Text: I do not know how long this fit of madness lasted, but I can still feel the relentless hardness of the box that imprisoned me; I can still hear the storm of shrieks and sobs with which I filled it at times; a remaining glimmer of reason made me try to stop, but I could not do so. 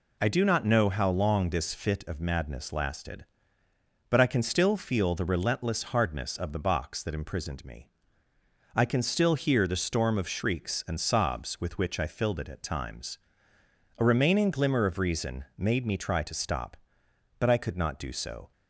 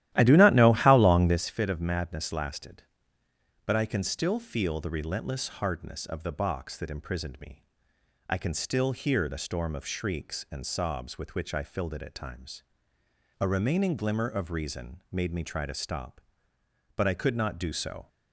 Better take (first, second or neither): first